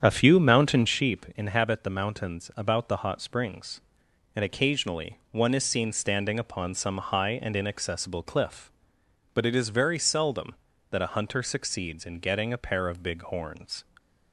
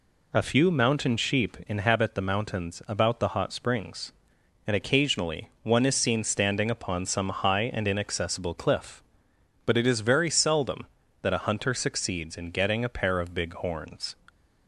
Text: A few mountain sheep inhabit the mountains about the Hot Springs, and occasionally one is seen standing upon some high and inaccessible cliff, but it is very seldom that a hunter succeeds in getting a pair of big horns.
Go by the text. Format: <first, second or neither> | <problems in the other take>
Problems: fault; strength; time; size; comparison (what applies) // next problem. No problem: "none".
second | starts louder than the rest; strong; until 1.1 s; 8 dB